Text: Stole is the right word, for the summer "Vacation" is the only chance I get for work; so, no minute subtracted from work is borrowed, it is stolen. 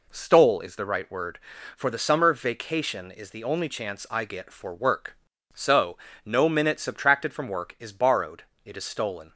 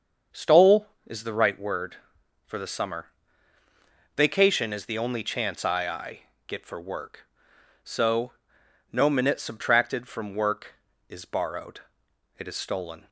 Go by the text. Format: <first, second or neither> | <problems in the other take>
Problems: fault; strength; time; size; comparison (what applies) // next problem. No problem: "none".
first | starts louder than the rest; until 1.5 s; 7 dB // pauses between "summer" and "Vacation"; at 3.0 s; 1.0 s long // says "I" twice; at 5.8 s